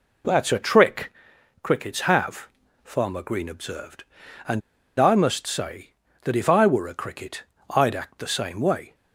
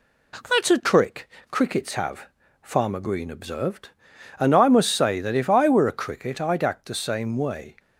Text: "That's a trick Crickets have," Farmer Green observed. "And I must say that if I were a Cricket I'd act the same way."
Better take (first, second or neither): second